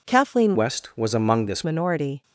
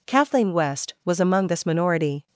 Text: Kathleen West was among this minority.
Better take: second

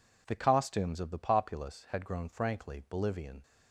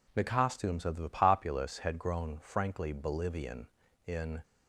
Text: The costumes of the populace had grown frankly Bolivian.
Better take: first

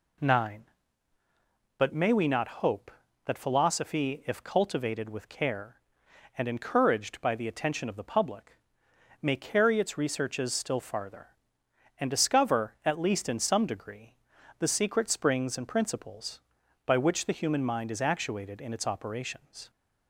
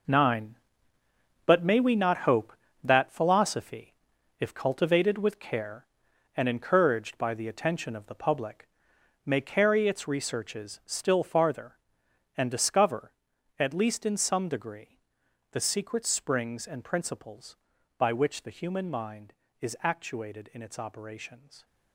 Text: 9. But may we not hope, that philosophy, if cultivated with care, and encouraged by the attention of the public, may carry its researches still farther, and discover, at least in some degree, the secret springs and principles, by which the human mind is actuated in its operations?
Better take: first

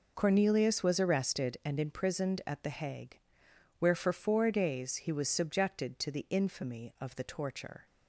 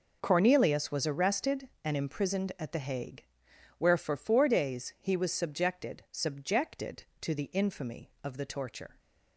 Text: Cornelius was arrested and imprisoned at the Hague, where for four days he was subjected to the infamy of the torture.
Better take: first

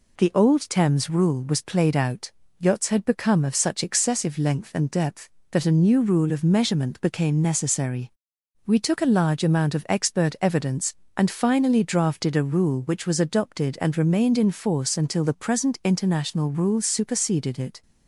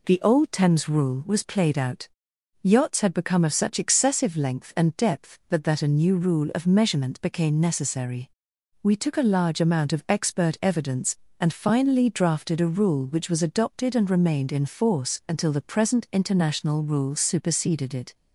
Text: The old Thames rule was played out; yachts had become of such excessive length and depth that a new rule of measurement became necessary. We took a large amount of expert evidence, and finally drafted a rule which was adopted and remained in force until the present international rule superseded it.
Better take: first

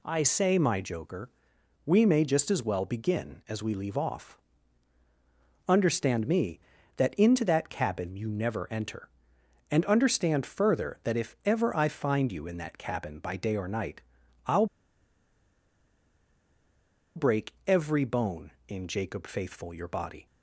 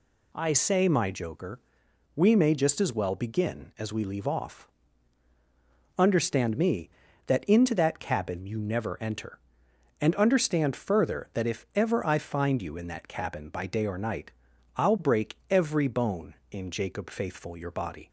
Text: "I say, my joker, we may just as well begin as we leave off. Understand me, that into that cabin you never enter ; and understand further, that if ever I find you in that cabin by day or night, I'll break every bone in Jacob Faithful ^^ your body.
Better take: second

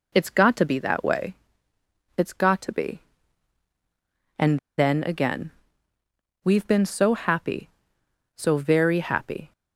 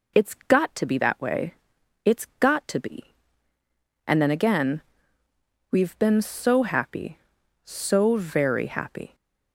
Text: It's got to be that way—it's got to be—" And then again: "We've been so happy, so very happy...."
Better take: second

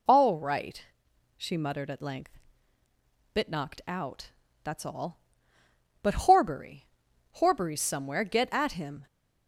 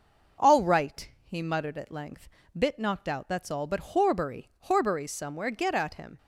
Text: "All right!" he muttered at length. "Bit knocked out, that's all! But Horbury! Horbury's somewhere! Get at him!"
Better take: second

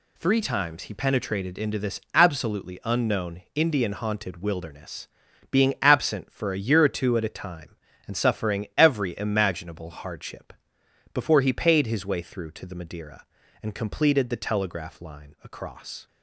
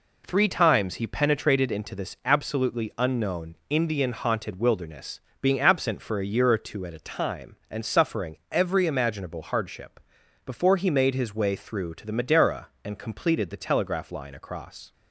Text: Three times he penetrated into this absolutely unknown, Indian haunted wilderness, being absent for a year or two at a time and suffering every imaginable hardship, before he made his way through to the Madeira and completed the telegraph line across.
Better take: second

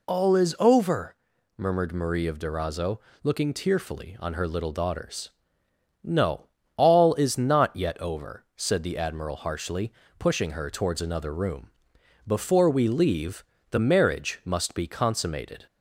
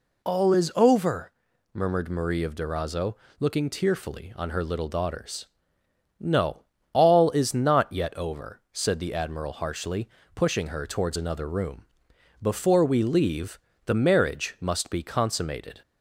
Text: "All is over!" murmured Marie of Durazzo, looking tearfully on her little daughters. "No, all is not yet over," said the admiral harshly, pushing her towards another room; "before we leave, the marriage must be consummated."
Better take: neither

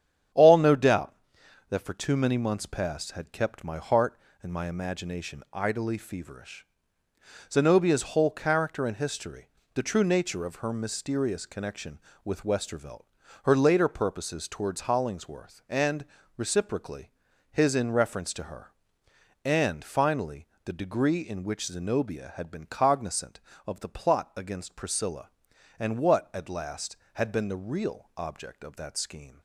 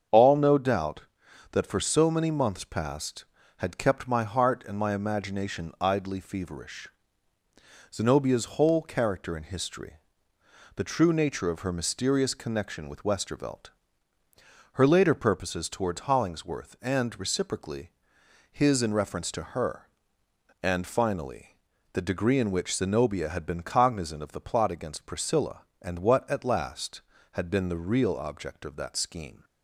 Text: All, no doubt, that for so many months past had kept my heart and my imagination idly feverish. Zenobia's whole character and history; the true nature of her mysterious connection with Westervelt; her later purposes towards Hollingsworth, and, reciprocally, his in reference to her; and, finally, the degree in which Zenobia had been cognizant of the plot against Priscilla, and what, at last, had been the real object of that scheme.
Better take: second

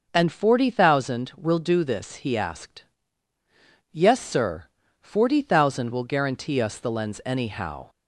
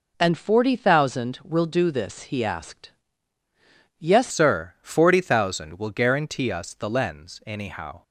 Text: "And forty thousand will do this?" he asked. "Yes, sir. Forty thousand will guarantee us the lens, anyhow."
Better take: first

